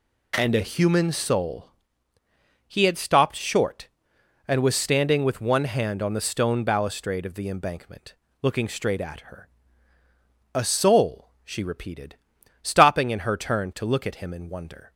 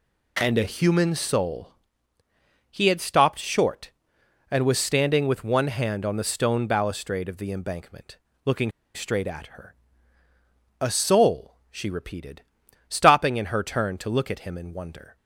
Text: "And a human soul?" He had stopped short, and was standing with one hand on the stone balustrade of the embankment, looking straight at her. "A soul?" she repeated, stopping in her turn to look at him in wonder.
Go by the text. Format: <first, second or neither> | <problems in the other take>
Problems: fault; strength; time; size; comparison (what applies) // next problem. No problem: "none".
first | pauses between "looking" and "straight"; slight; at 8.6 s; 0.25 s long